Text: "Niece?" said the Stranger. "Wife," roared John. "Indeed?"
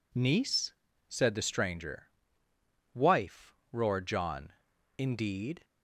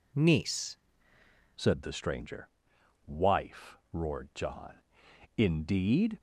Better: first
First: none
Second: changes voice at "said"; from 1.5 s on; 4.6 s long

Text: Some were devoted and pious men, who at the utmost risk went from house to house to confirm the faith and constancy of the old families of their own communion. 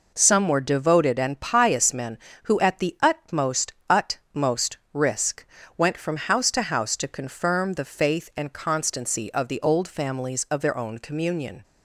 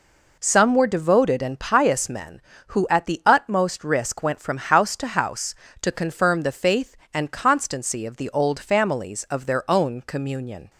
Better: second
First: says "utmost" twice; at 3.8 s // pauses between "risk" and "went"; slight; at 5.4 s; 0.34 s long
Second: none

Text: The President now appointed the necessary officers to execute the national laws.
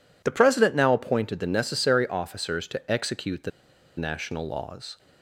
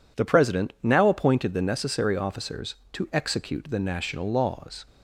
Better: second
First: pauses between "the" and "national"; noticeable; at 3.5 s; 0.47 s long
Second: none

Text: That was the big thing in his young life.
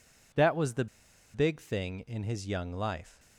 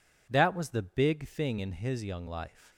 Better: second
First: pauses between "the" and "big"; noticeable; at 0.8 s; 0.47 s long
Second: none

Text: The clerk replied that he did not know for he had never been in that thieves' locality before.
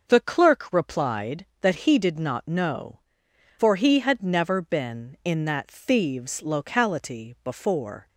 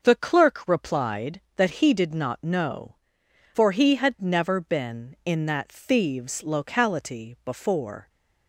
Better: neither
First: starts louder than the rest; noticeable; until 1.0 s; 6 dB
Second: starts louder than the rest; noticeable; until 1.0 s; 6 dB

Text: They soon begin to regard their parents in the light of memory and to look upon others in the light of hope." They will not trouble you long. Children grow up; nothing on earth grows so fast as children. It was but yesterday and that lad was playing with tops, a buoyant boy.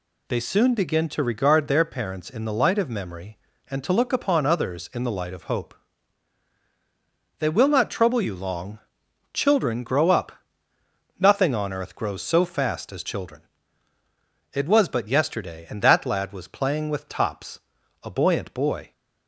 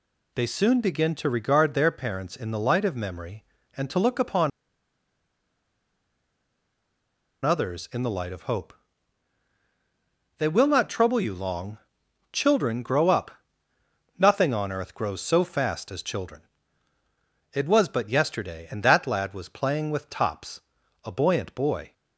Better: first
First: none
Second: pauses between "upon" and "others"; strong; at 4.5 s; 2.9 s long

